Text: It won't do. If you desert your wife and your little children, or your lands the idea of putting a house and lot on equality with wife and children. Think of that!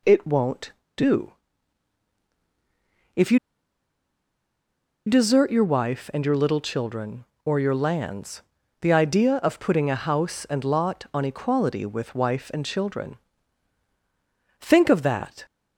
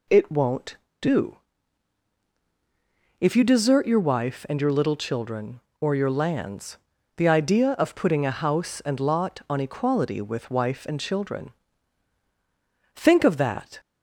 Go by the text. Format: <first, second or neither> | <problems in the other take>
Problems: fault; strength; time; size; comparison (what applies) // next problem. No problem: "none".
second | pauses between "you" and "desert"; strong; at 3.3 s; 1.6 s long // pauses between "lands" and "the"; at 8.4 s; 0.40 s long; also in the second